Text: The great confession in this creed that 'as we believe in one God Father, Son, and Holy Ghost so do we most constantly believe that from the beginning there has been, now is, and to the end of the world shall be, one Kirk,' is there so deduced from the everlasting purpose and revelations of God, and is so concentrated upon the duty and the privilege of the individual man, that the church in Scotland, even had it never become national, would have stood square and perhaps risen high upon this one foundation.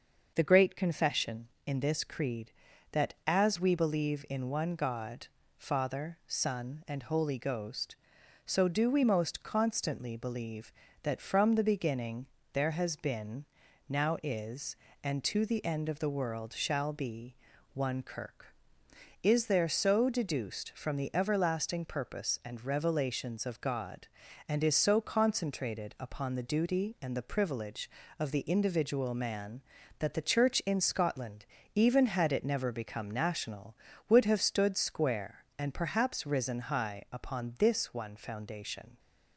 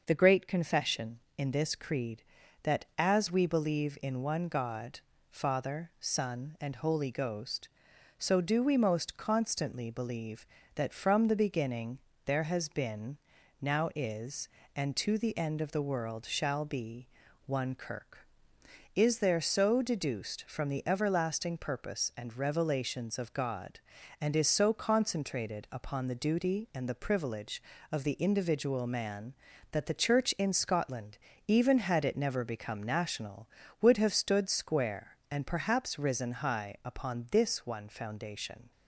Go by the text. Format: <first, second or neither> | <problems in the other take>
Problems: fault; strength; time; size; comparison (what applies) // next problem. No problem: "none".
neither | starts louder than the rest; the same in both // pauses between "God" and "Father"; slight; the same in both // pauses between "beginning" and "there"; slight; the same in both